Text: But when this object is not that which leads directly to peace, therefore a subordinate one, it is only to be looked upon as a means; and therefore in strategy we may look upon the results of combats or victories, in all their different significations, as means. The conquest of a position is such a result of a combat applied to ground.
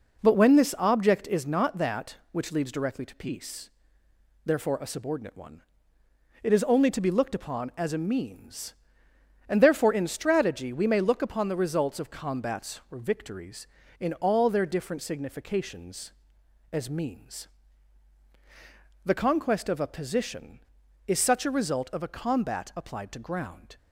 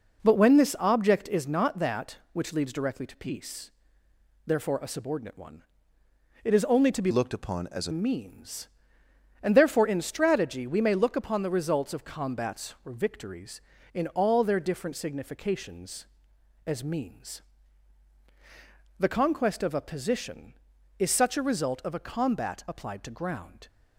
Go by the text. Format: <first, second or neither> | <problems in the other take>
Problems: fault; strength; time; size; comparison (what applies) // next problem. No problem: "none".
first | changes voice from "looked" to "a"; from 7.0 to 7.9 s; 0.9 s long